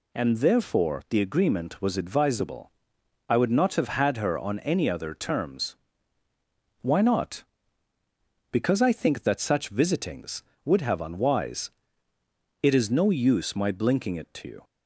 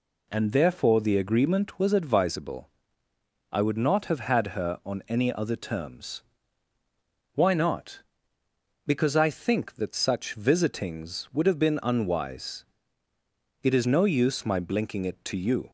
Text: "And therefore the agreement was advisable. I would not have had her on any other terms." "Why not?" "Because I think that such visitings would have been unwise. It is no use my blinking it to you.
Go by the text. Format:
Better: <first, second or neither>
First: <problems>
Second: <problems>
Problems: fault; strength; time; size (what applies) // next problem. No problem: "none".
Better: second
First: skips "been"; at 11.0 s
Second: none